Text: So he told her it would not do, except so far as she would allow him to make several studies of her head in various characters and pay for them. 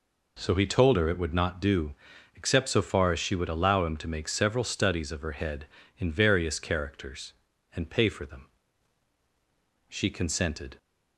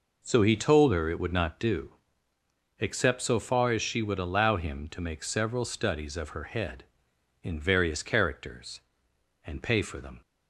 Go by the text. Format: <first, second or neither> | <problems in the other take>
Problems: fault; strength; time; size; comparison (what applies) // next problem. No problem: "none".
second | goes on to say "She consented"; noticeable; from 9.8 s on; 0.88 s long